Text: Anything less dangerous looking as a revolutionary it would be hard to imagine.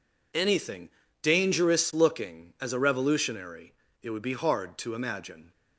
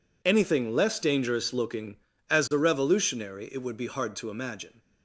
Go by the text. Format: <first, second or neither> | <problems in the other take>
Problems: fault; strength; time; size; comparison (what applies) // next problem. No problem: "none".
second | skips "less"; at 1.0 s // pauses between "revolutionary" and "it"; slight; at 3.7 s; 0.28 s long